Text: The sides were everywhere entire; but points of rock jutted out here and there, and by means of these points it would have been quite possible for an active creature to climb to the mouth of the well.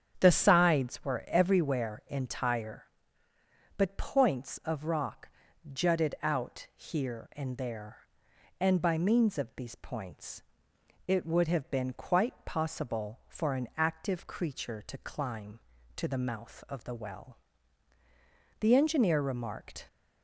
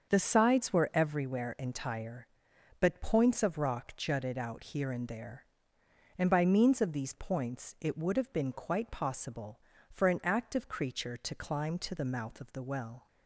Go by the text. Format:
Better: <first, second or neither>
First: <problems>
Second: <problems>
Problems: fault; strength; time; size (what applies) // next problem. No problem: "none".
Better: second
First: starts louder than the rest; strong; until 1.2 s; 8.5 dB // pauses between "rock" and "jutted"; noticeable; at 5.2 s; 0.46 s long // pauses between "points" and "it"; noticeable; at 10.4 s; 0.64 s long // goes on to say "The engineer remarked"; noticeable; from 18.5 s on; 1.2 s long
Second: starts louder than the rest; until 1.1 s; 6.5 dB